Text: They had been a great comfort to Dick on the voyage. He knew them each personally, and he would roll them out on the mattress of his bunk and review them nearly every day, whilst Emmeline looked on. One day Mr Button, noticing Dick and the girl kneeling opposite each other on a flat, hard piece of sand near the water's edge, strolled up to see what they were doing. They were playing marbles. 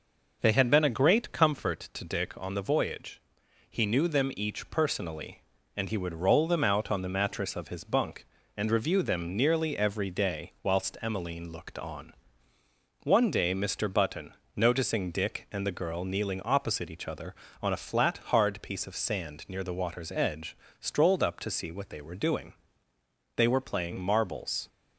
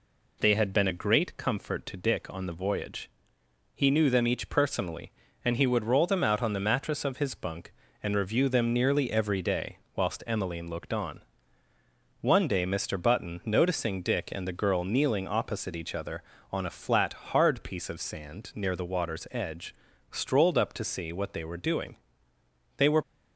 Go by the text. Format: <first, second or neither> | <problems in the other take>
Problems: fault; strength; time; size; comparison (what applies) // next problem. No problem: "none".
first | stops before "playing marbles"; at 23.0 s